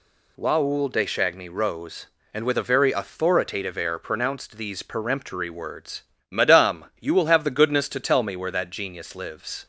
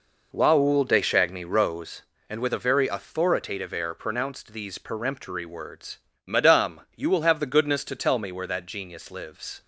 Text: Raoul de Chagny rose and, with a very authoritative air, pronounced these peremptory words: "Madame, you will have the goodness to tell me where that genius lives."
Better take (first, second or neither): first